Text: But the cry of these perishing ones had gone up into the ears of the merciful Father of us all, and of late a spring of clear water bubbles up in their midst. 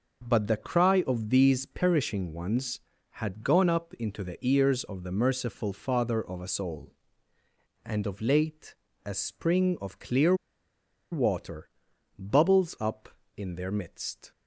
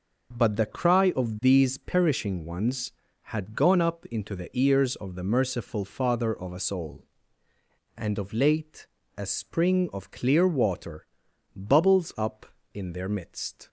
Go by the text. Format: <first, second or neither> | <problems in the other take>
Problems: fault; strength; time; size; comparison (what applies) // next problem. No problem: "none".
second | starts louder than the rest; noticeable; until 1.3 s; 6 dB; noticeable in the second // pauses between "late" and "a"; slight; at 8.7 s; 0.30 s long; slight in the second // pauses between "clear" and "water"; noticeable; at 10.3 s; 0.77 s long // pauses between "water" and "bubbles"; noticeable; at 11.6 s; 0.48 s long; noticeable in the second